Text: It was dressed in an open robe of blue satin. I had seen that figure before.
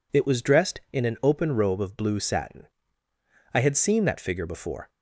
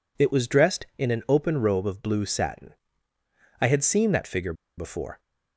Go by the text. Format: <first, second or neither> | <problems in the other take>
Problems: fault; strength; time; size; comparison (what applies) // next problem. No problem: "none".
first | pauses between "figure" and "before"; slight; at 4.5 s; 0.24 s long